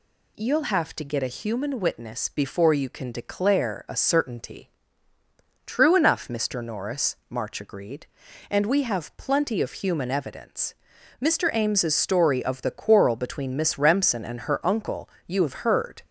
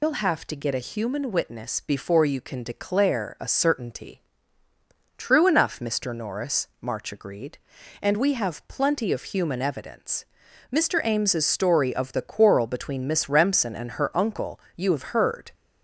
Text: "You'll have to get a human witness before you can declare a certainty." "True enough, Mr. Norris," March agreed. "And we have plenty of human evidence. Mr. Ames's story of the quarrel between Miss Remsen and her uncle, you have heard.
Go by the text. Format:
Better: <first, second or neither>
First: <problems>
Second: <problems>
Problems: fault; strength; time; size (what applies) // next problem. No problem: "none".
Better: first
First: none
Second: loses the start of "You'll"; at 0.0 s; 155 ms